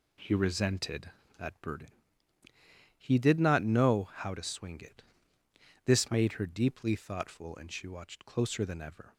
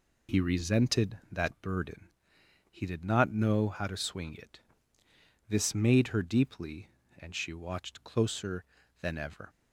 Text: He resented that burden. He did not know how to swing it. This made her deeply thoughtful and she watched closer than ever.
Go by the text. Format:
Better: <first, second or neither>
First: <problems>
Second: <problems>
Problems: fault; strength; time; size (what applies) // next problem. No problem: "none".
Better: first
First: none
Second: skips "thoughtful"; at 7.0 s